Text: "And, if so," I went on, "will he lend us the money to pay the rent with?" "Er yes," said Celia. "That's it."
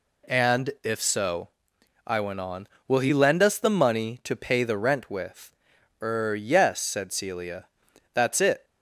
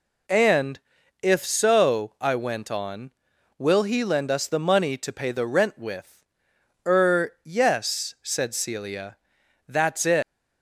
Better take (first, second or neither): first